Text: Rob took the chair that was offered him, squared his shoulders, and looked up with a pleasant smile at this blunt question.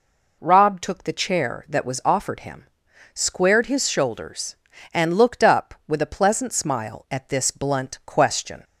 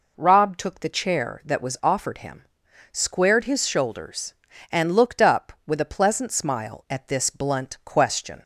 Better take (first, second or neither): neither